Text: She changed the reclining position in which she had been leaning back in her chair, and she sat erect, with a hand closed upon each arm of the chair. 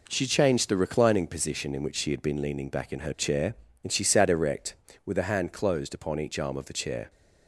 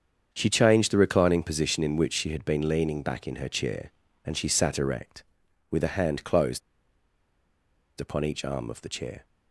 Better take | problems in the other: first | starts louder than the rest; strong; until 1.3 s; 7.5 dB // pauses between "closed" and "upon"; strong; at 6.6 s; 1.3 s long

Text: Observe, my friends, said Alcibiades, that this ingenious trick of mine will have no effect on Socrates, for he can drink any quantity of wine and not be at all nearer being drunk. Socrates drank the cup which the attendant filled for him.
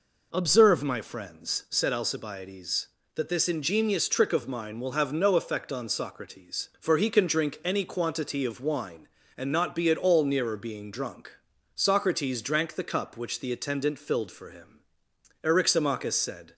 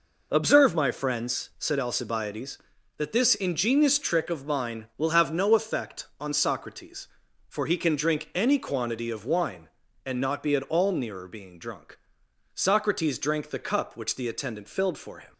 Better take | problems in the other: second | goes on to say "Eryximachus said"; noticeable; from 15.4 s on; 1.1 s long

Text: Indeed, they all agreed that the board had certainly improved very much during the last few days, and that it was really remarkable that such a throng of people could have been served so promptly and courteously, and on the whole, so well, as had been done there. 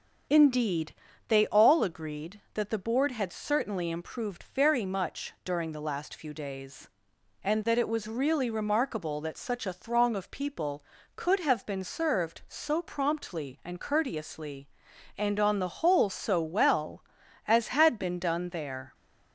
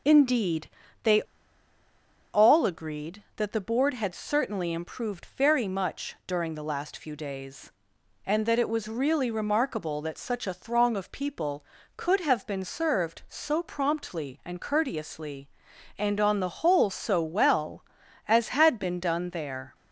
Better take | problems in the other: first | starts louder than the rest; until 2.5 s; 6.5 dB; also in the first // pauses between "they" and "all"; at 1.2 s; 1.1 s long

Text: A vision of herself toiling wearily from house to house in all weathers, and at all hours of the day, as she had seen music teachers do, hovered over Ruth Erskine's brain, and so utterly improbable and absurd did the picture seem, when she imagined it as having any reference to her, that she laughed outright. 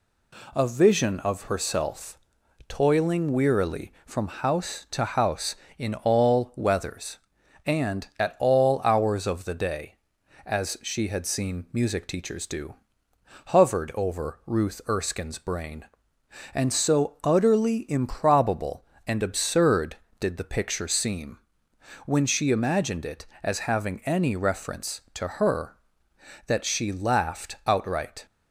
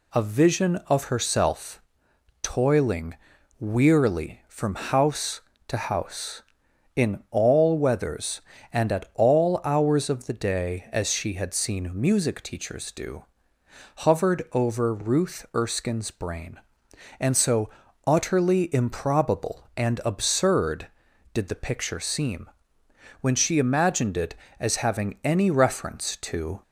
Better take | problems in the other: first | pauses between "herself" and "toiling"; noticeable; at 1.8 s; 0.60 s long; noticeable in the first // pauses between "toiling" and "wearily"; noticeable; at 3.1 s; 0.46 s long // pauses between "so" and "utterly"; slight; at 17.6 s; 0.34 s long // stops before "her that she laughed outright"; at 26.6 s

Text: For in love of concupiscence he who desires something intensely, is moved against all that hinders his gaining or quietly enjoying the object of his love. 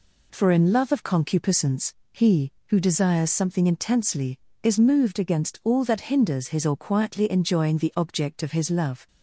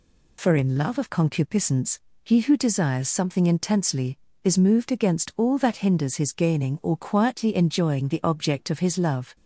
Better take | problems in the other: second | pauses between "concupiscence" and "he"; slight; at 1.9 s; 0.20 s long; slight in the second // skips "gaining"; at 6.6 s

